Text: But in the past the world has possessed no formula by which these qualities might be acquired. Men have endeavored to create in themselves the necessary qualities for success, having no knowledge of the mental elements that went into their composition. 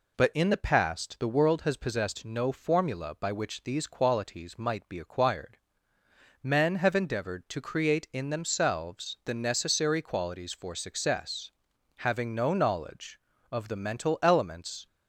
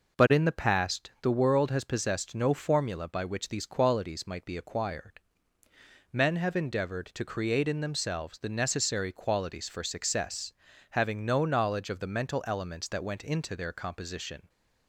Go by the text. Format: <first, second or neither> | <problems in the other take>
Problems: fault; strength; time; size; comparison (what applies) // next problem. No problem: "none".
second | stops before "that went into their composition"; at 14.8 s